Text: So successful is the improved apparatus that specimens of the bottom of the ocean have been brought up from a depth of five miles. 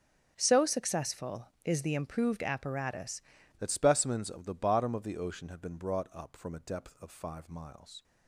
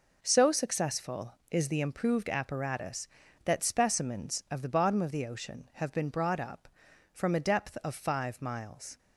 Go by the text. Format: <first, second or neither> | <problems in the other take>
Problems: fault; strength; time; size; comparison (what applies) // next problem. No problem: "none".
second | starts louder than the rest; until 1.3 s; 6.5 dB // changes voice at "that"; from 3.5 s on; 4.5 s long